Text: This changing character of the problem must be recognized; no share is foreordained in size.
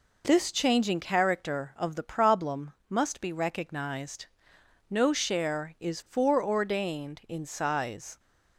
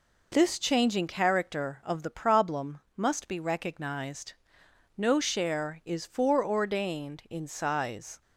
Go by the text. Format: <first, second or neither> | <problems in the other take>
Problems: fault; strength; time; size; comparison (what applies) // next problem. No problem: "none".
neither | pauses between "problem" and "must"; slight; the same in both